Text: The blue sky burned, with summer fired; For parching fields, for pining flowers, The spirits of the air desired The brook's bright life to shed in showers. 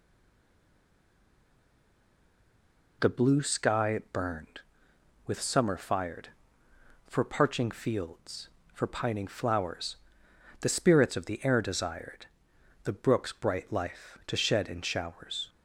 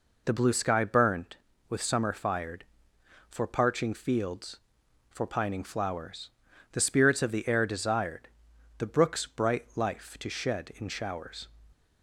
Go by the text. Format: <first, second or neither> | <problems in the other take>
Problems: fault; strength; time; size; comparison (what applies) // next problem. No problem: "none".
second | stays silent before the first word; strong; until 3.0 s; 3.0 s long // pauses between "desired" and "The"; noticeable; at 12.2 s; 0.58 s long; noticeable in the second